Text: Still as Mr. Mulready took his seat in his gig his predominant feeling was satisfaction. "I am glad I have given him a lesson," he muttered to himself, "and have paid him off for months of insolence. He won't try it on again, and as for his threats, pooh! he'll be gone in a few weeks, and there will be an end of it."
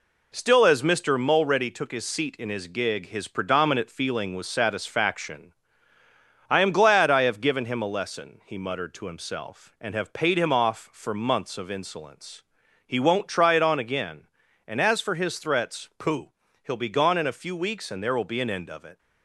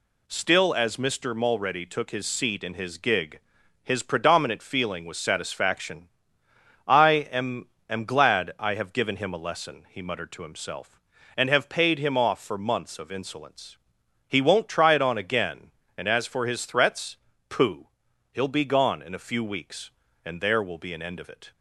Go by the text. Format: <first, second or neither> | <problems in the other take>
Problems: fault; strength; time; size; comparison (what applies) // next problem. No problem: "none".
first | pauses between "gig" and "his"; at 3.3 s; 0.44 s long // says "am" twice; at 7.8 s